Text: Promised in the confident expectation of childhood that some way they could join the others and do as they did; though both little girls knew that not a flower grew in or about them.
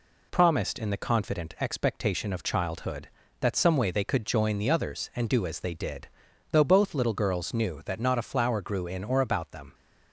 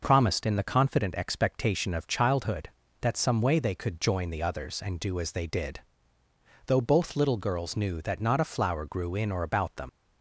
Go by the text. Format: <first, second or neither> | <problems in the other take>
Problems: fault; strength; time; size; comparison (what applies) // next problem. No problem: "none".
first | leaves "them" unfinished; at 9.8 s; 60 ms